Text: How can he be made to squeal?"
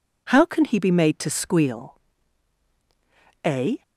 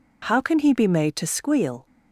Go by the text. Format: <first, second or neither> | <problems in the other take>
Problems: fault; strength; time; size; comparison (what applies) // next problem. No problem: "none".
second | goes on to say "A"; slight; from 3.4 s on; 0.38 s long